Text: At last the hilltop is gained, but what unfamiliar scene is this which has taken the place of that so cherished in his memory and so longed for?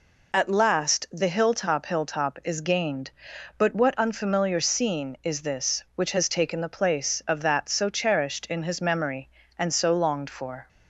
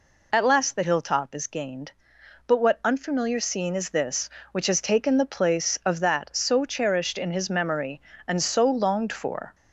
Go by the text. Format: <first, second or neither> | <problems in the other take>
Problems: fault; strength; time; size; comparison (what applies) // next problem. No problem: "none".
second | says "hilltop" twice; at 1.8 s